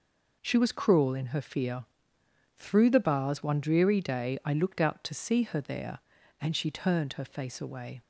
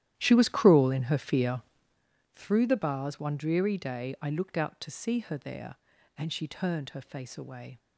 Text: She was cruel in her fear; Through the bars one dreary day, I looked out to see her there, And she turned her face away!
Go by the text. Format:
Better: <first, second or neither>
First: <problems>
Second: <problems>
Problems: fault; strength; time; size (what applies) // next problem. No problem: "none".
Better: first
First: none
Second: starts louder than the rest; strong; until 2.1 s; 12 dB